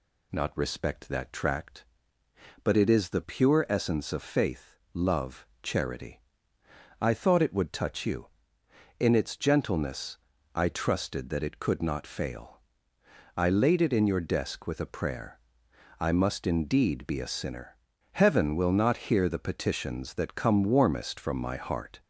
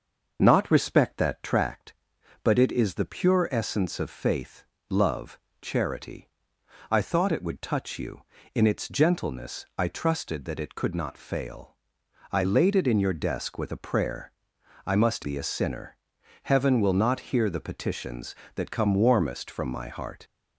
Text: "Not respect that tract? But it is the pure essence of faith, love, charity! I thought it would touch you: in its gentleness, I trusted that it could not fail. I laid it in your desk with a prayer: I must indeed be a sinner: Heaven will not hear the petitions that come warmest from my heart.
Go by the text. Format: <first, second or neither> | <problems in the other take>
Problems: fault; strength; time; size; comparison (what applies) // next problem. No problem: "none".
first | starts louder than the rest; noticeable; until 1.4 s; 6 dB // skips "indeed"; at 15.2 s